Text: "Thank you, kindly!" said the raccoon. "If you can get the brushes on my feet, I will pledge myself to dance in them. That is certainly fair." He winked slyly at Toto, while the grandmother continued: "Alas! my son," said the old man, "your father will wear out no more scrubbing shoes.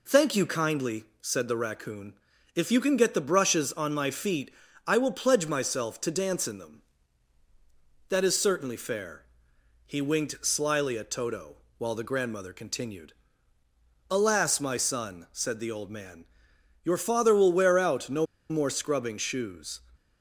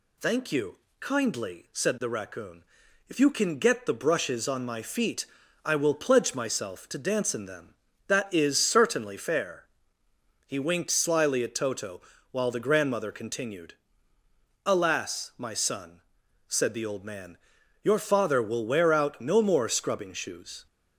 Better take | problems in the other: second | pauses between "no" and "more"; slight; at 18.2 s; 0.24 s long

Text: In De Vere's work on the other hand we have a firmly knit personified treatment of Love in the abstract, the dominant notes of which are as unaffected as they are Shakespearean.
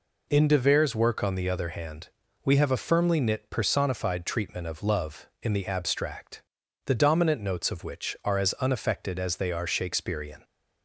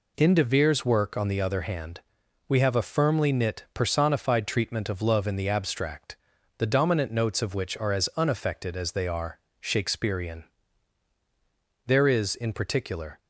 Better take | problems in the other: first | pauses between "hand" and "we"; noticeable; at 1.9 s; 0.48 s long; slight in the first // pauses between "are" and "Shakespearean"; slight; at 9.3 s; 0.20 s long // goes on to say "There is in particular"; from 11.8 s on; 1.3 s long

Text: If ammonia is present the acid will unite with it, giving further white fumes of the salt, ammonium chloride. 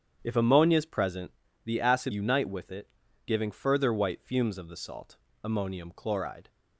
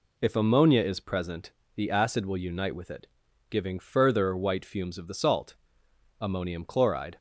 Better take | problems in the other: second | starts louder than the rest; strong; until 1.2 s; 8.5 dB // pauses between "present" and "the"; slight; at 1.3 s; 0.34 s long; slight in the second // skips "will"; at 2.1 s

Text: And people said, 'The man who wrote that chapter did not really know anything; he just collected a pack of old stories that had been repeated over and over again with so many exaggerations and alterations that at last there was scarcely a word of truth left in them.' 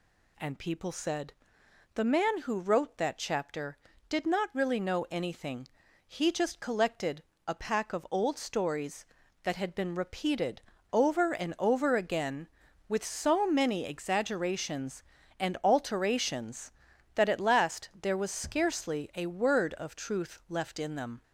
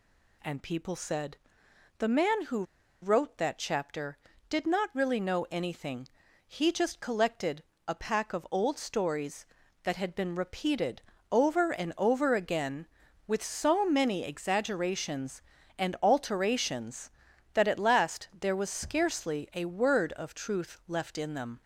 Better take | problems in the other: first | pauses between "who" and "wrote"; at 2.6 s; 0.39 s long // pauses between "collected" and "a"; slight; at 7.6 s; 0.24 s long; slight in the first // pauses between "repeated" and "over"; slight; at 11.0 s; 0.30 s long; slight in the first

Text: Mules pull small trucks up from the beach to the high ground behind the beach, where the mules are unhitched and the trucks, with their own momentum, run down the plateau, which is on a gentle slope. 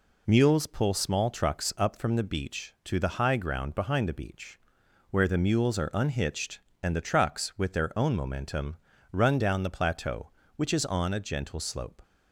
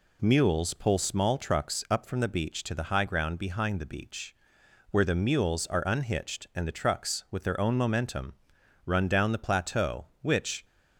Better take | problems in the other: first | stops before "is on a gentle slope"; at 10.6 s

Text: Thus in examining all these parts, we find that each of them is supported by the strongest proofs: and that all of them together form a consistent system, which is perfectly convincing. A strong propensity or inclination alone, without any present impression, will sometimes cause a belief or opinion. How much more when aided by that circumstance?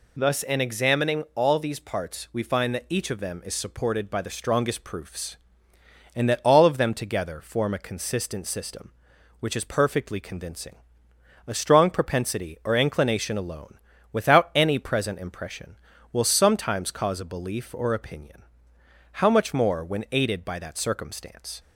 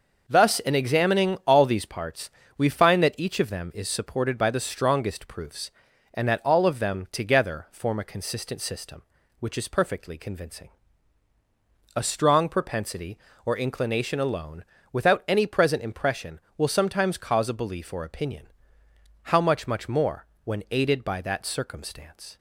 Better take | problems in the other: first | says "much" twice; at 19.6 s // pauses between "more" and "when"; slight; at 20.2 s; 0.18 s long

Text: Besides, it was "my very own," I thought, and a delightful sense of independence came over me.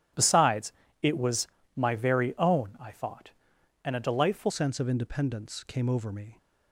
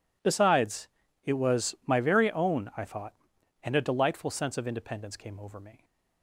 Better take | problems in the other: second | starts louder than the rest; strong; until 1.4 s; 11.5 dB // pauses between "was" and "my"; slight; at 1.4 s; 0.28 s long // changes voice at "sense"; from 4.5 s on; 1.8 s long

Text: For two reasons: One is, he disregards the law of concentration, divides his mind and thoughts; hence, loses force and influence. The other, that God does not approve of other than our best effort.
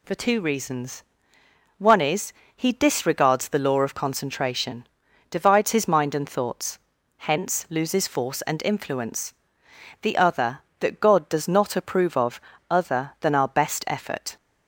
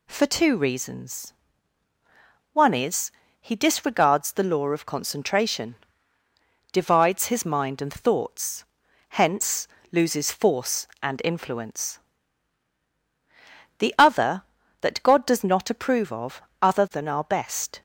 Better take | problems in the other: first | pauses between "of" and "other"; slight; at 16.3 s; 0.22 s long; slight in the first // stops before "effort"; at 17.7 s

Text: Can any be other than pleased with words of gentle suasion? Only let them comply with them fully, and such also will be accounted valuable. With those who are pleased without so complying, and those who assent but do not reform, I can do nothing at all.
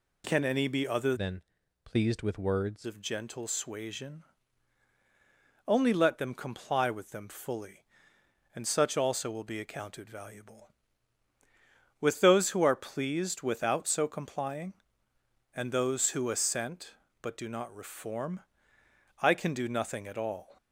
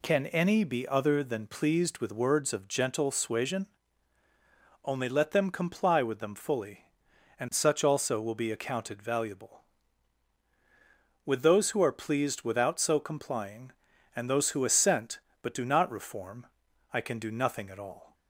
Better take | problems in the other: second | changes voice from "than" to "words"; from 1.1 to 2.8 s; 1.7 s long // pauses between "than" and "pleased"; at 1.4 s; 0.42 s long

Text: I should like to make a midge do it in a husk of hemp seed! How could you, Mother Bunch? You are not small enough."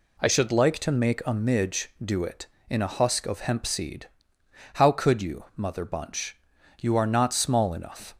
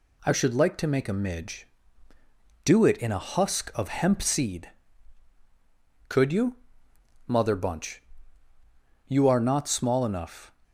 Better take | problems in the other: first | skips "How"; at 5.3 s

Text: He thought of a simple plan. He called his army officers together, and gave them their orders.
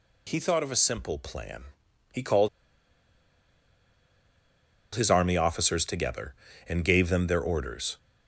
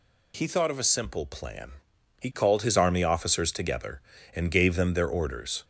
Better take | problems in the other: second | pauses between "called" and "his"; strong; at 2.4 s; 2.4 s long

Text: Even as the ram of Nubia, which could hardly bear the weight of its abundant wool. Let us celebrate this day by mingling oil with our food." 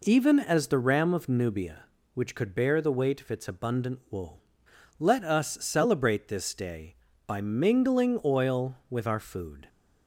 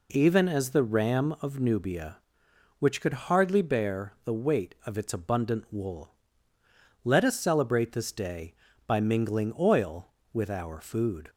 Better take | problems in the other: second | skips "hardly"; at 2.5 s

